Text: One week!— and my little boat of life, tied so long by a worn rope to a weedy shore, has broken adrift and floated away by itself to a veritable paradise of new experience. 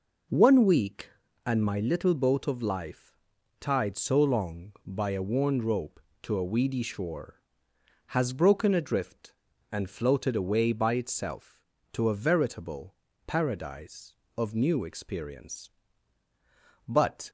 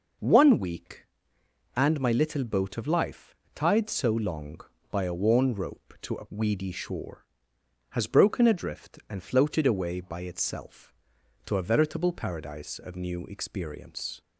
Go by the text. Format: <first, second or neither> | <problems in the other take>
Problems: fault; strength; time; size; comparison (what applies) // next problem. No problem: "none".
second | pauses between "veritable" and "paradise"; slight; at 12.9 s; 0.32 s long // goes on to say "But"; slight; from 16.8 s on; 0.42 s long